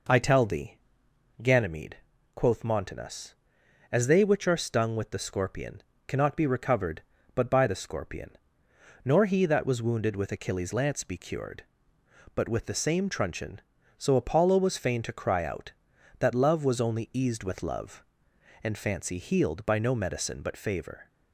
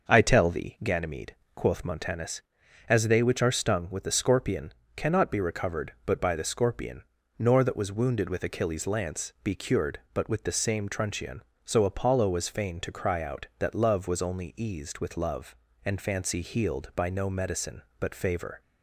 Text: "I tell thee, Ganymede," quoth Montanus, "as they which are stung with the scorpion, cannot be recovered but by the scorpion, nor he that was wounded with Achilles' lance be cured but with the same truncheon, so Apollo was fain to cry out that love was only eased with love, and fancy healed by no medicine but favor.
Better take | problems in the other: first | starts louder than the rest; until 1.1 s; 6 dB // skips "he"; at 7.6 s

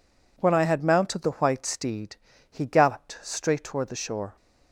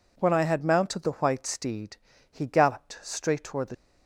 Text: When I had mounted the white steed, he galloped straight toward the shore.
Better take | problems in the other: first | stops before "shore"; at 3.7 s

